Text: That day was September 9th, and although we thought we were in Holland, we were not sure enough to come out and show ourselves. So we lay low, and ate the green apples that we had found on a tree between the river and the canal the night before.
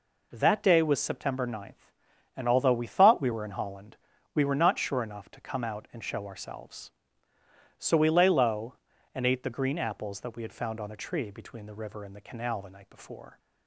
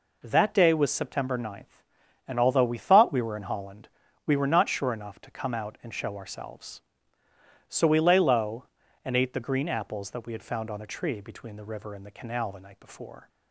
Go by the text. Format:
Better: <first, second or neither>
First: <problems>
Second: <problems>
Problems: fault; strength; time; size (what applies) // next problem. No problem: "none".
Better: neither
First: none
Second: none